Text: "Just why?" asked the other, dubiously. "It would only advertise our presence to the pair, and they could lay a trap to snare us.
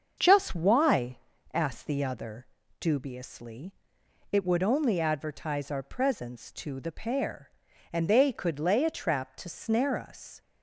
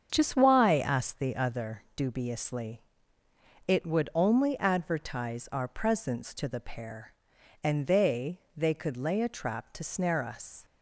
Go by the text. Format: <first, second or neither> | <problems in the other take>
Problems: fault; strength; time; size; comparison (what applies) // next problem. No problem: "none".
first | starts louder than the rest; strong; until 1.1 s; 7.5 dB; also in the first // says "they" twice; at 8.5 s